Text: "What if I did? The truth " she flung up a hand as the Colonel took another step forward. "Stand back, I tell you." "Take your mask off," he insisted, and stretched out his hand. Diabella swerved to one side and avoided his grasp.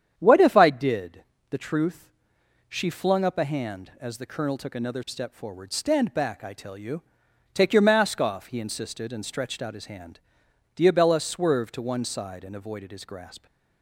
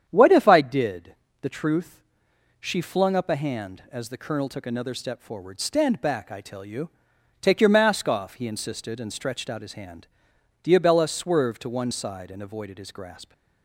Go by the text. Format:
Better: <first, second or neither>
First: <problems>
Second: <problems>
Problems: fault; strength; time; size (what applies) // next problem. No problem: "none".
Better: neither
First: starts louder than the rest; strong; until 1.1 s; 9 dB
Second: starts louder than the rest; strong; until 1.0 s; 9 dB